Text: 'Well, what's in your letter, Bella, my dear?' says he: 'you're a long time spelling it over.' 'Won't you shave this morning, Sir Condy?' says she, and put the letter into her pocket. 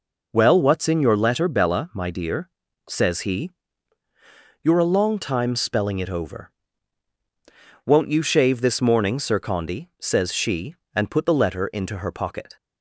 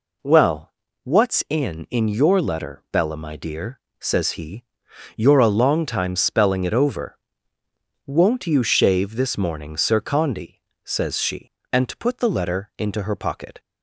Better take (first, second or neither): first